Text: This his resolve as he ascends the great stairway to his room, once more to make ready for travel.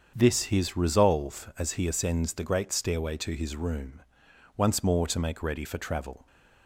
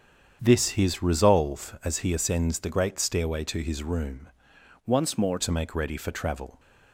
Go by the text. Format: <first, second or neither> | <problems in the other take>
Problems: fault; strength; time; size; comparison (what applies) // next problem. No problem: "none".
first | starts louder than the rest; strong; until 1.4 s; 8 dB; strong in the first // changes voice from "once" to "more"; from 4.8 to 5.3 s; 0.5 s long